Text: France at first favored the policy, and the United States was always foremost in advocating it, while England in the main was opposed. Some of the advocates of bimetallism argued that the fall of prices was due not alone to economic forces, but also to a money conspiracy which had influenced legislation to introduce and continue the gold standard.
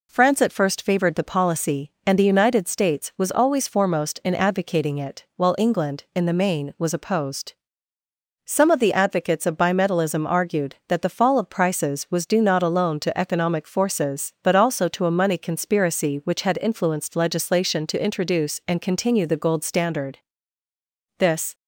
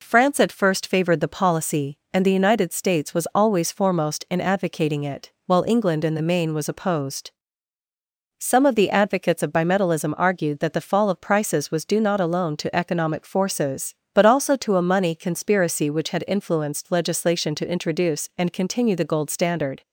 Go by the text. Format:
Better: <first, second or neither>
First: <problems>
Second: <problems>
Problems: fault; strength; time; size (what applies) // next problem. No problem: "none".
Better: second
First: goes on to say "This"; slight; from 21.1 s on; 0.36 s long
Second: none